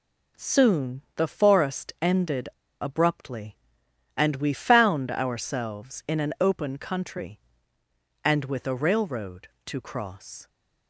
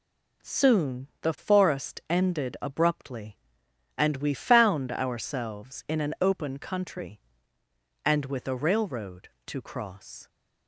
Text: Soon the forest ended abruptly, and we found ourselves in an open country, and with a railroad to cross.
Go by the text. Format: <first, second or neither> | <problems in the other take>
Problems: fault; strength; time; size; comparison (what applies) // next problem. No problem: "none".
second | pauses between "ended" and "abruptly"; slight; at 2.4 s; 0.32 s long